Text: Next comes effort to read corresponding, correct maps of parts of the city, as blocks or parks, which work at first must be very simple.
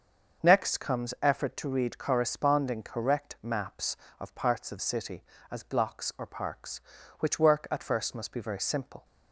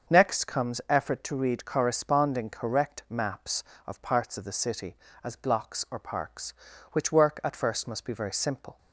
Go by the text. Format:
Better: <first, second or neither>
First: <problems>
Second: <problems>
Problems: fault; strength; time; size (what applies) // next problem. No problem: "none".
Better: second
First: starts louder than the rest; until 1.5 s; 6.5 dB // skips "the"; at 4.7 s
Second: starts louder than the rest; until 1.1 s; 6.5 dB